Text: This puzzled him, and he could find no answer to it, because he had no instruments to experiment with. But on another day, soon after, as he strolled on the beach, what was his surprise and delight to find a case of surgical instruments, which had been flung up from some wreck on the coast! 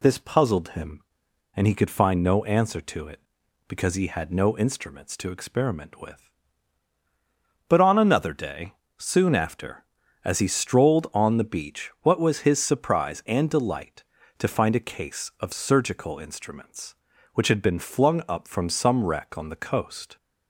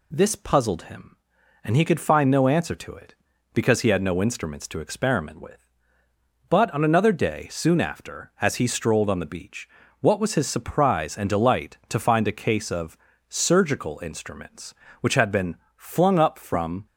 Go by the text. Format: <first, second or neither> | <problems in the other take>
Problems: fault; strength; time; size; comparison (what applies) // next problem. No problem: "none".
first | pauses between "of" and "surgical"; slight; at 12.9 s; 0.32 s long // pauses between "been" and "flung"; slight; at 15.5 s; 0.22 s long // stops before "some wreck on the coast"; at 16.8 s